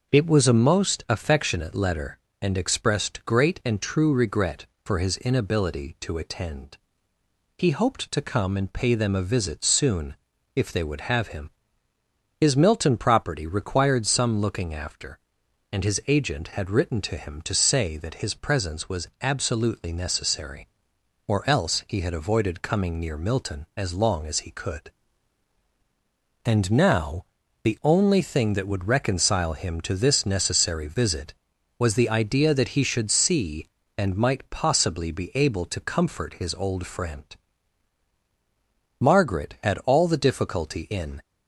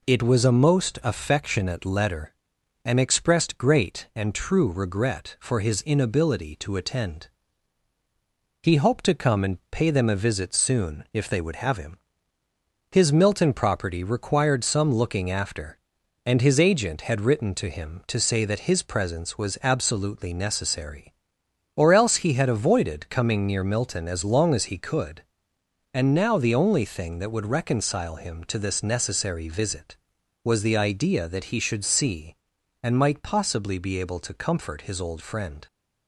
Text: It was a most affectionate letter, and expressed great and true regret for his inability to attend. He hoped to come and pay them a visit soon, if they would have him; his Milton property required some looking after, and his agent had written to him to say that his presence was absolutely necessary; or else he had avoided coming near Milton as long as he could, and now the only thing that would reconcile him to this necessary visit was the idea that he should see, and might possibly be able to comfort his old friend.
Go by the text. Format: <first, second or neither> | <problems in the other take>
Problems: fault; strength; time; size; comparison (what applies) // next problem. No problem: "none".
second | starts louder than the rest; until 1.1 s; 6.5 dB // pauses between "now" and "the"; at 27.2 s; 0.40 s long // goes on to say "Margaret had all the difficulty in"; strong; from 39.0 s on; 2.2 s long